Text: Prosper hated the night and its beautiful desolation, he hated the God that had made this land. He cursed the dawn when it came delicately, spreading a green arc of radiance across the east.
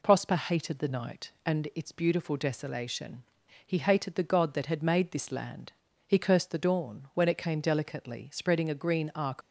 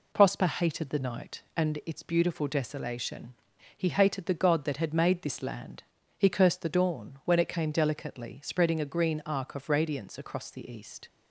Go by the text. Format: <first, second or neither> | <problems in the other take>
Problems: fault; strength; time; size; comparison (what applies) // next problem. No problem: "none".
second | stops before "of radiance across the east"; at 9.4 s